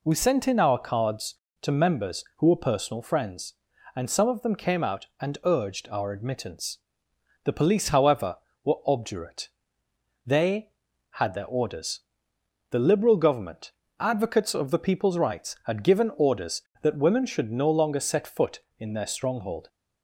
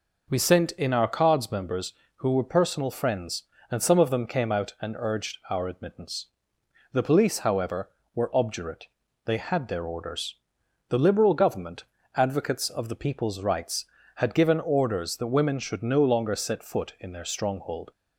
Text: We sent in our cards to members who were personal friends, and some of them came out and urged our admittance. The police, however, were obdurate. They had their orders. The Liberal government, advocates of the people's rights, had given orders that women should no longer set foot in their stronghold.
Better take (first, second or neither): first